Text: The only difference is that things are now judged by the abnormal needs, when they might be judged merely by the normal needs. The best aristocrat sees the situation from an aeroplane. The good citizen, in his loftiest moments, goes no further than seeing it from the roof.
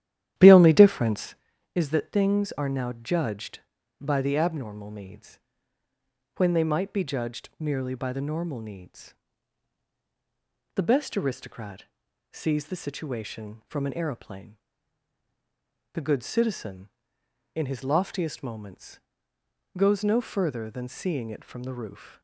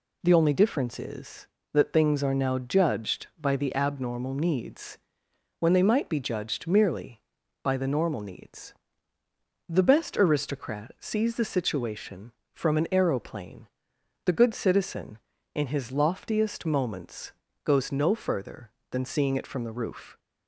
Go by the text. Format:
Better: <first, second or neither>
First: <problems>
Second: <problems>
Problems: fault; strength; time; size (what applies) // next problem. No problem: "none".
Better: second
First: starts louder than the rest; strong; until 1.4 s; 12 dB // pauses between "aristocrat" and "sees"; noticeable; at 11.8 s; 0.48 s long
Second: none